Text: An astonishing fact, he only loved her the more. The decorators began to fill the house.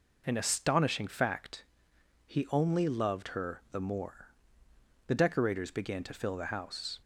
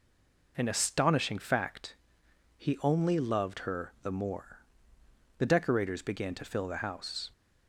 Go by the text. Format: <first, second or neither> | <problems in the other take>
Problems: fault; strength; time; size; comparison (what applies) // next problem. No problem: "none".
first | stays silent before the first word; slight; until 0.5 s; 0.5 s long